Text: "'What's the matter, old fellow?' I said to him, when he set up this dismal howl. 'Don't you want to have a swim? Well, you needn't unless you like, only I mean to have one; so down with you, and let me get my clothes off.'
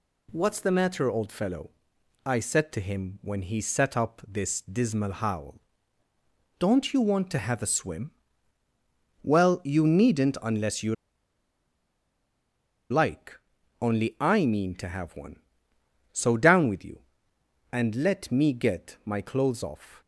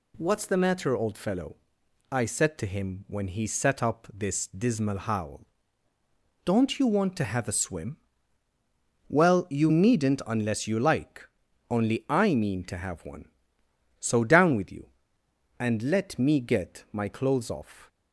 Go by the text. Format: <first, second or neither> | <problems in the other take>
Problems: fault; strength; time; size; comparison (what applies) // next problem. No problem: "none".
second | pauses between "you" and "like"; strong; at 10.9 s; 1.9 s long